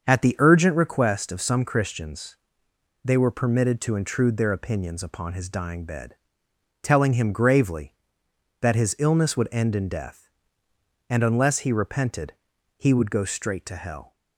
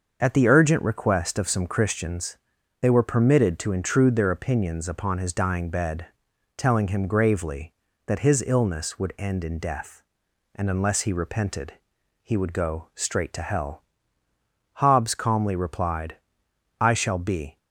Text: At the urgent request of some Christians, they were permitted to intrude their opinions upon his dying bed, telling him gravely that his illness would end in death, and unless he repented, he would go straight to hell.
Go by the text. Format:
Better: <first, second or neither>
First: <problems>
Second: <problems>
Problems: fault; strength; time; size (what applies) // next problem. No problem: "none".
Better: first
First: starts louder than the rest; until 1.0 s; 7 dB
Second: starts louder than the rest; until 1.2 s; 6.5 dB // goes on to say "Hobbes calmly replied I shall be"; strong; from 14.7 s on; 2.8 s long